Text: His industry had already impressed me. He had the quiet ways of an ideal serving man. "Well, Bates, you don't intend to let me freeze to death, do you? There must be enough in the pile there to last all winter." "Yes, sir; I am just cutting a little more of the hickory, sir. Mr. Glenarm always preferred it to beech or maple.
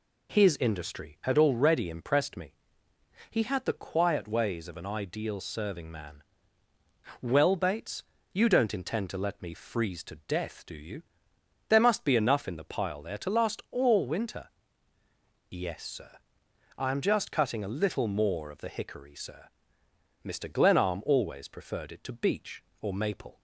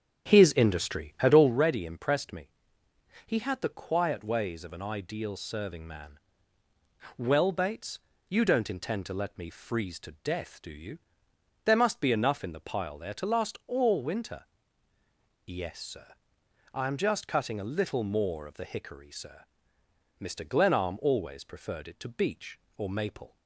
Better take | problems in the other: first | starts louder than the rest; strong; until 1.6 s; 9 dB

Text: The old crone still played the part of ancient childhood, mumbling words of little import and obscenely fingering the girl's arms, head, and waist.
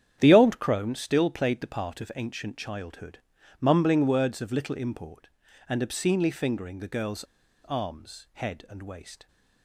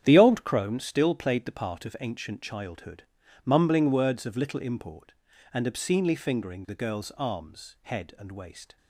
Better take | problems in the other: second | starts louder than the rest; strong; until 1.2 s; 9 dB; strong in the second // pauses between "girl's" and "arms"; at 7.2 s; 0.40 s long

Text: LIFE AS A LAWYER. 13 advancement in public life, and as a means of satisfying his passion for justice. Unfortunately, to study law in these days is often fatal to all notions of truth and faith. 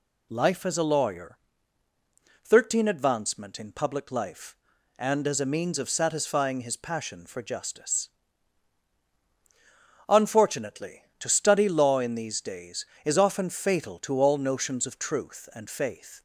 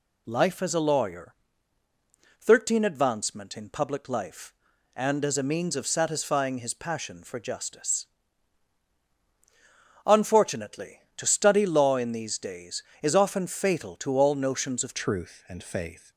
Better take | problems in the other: first | changes voice at "truth"; from 14.9 s on; 1.2 s long

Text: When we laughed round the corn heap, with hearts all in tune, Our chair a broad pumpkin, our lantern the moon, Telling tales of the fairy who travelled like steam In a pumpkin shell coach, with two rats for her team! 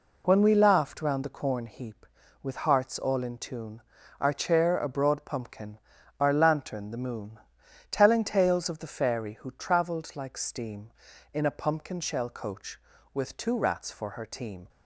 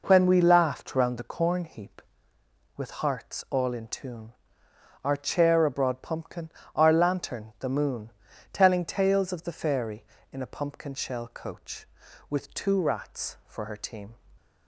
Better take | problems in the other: first | skips "who travelled like steam"; at 10.1 s

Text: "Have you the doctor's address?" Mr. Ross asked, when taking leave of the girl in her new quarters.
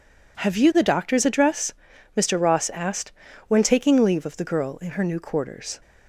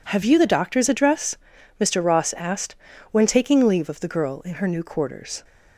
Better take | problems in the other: neither | none

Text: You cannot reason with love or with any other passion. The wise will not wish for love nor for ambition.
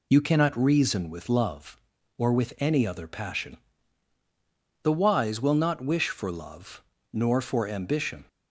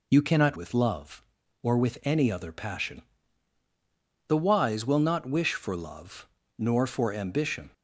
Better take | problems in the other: first | skips "reason"; at 0.5 s // pauses between "love" and "nor"; slight; at 6.2 s; 0.30 s long; slight in the first

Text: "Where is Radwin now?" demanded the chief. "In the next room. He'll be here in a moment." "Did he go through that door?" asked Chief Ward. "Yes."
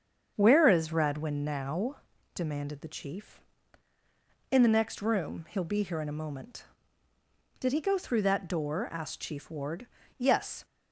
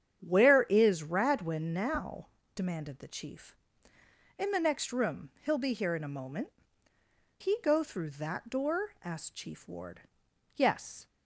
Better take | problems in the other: first | starts louder than the rest; strong; until 1.2 s; 8.5 dB; strong in the first // skips "Did"; at 6.9 s

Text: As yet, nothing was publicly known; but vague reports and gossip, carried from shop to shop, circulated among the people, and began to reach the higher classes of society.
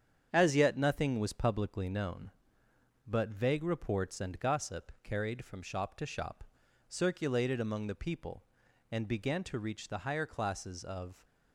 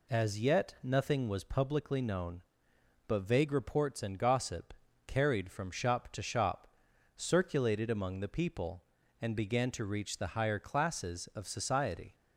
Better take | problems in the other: second | starts louder than the rest; strong; until 1.3 s; 8 dB // stops before "society"; at 11.2 s

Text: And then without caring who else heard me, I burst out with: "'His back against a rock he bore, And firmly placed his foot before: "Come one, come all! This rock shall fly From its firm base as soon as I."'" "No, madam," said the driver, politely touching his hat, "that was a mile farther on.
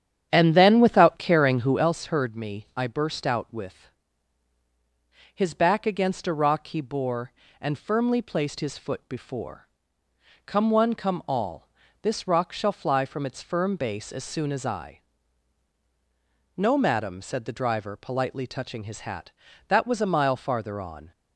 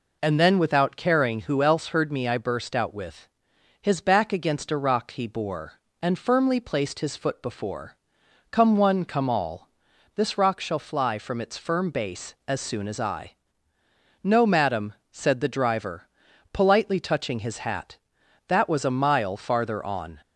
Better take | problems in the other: second | starts louder than the rest; strong; until 1.9 s; 9.5 dB

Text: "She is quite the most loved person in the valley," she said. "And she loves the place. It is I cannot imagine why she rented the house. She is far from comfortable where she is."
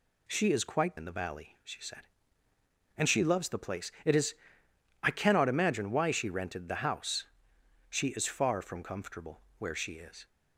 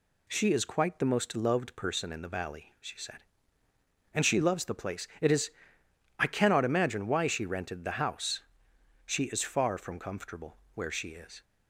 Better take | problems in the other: second | skips "the most loved person"; at 0.9 s // pauses between "is" and "I"; noticeable; at 4.3 s; 0.70 s long; noticeable in the second // pauses between "comfortable" and "where"; slight; at 9.4 s; 0.16 s long; slight in the second

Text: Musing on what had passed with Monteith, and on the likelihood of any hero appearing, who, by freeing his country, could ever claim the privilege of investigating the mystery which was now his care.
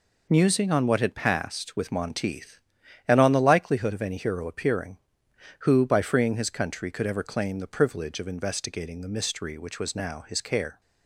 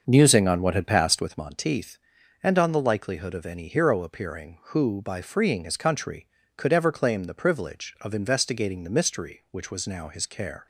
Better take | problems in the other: first | starts louder than the rest; until 1.5 s; 6 dB

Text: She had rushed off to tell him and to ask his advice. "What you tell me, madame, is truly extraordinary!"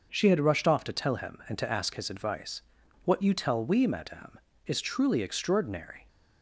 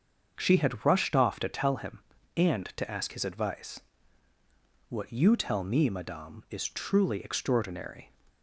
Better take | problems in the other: second | starts louder than the rest; until 1.1 s; 6 dB; also in the second // says "we" for "me"; at 3.6 s

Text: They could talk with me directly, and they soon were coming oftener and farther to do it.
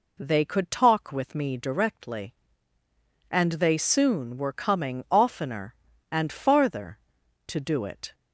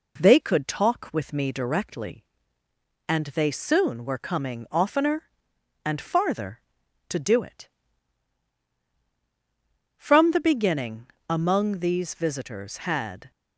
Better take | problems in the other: first | goes on to say "From the beginning among these visitors had"; strong; from 9.9 s on; 3.3 s long

